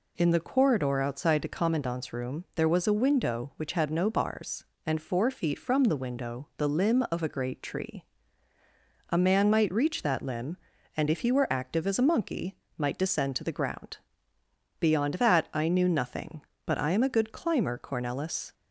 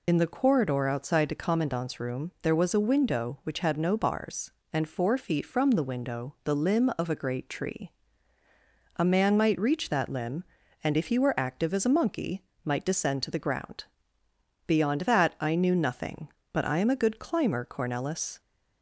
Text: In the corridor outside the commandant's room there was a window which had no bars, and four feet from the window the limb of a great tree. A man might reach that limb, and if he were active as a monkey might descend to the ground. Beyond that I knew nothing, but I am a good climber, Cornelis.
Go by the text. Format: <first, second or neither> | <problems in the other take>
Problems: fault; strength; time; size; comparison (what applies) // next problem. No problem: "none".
first | loses the start of "In"; at 0.0 s; 40 ms // pauses between "monkey" and "might"; slight; at 12.4 s; 0.22 s long; slight in the first